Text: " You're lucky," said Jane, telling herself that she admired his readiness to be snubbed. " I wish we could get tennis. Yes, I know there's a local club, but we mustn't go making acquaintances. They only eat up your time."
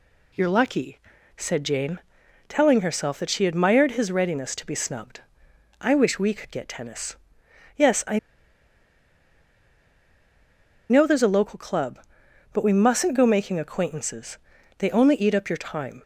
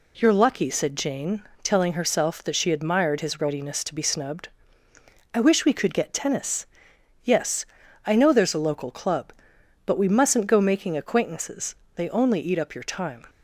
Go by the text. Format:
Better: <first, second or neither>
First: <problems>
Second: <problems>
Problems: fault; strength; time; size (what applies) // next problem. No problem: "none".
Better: second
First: pauses between "I" and "know"; strong; at 8.1 s; 2.7 s long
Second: none